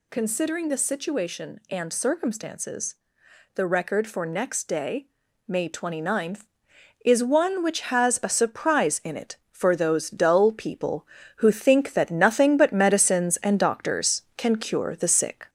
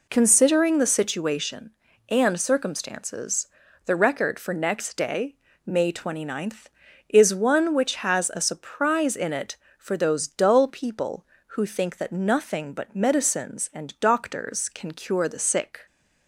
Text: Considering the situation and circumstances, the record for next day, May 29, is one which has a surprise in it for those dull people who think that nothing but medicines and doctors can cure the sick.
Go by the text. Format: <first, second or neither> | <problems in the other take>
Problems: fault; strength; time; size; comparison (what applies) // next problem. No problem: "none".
second | gets louder; slight; throughout; 3 dB